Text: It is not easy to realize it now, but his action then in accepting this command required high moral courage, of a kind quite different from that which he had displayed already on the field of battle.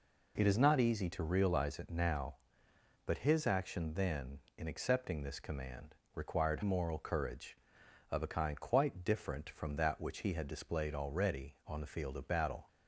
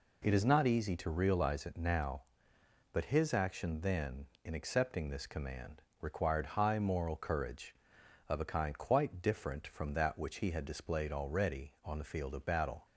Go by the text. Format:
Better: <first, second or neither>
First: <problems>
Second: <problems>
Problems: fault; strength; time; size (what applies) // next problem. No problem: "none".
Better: second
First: pauses between "command" and "required"; slight; at 5.9 s; 0.20 s long // skips "high"; at 6.6 s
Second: pauses between "command" and "required"; slight; at 5.8 s; 0.19 s long